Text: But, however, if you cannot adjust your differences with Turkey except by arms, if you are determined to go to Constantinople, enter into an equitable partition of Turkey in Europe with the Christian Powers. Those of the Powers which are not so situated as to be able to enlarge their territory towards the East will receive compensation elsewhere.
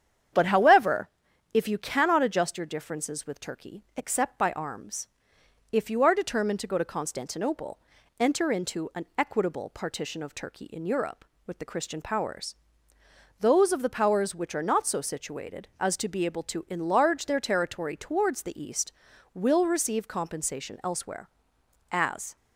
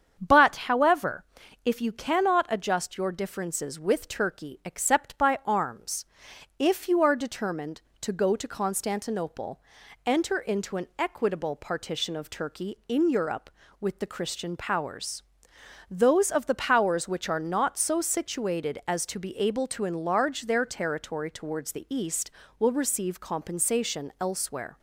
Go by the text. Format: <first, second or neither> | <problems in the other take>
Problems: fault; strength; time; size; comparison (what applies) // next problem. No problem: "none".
second | starts louder than the rest; strong; until 1.8 s; 8.5 dB; strong in the second // goes on to say "As"; slight; from 21.9 s on; 0.44 s long